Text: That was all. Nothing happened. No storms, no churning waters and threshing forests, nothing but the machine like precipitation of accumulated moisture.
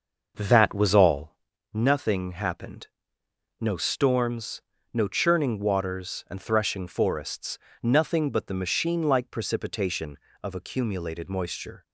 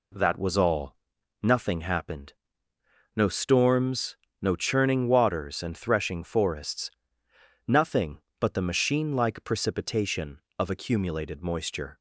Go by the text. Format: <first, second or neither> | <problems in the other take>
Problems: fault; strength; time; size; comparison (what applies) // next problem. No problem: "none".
second | starts louder than the rest; noticeable; until 1.4 s; 6 dB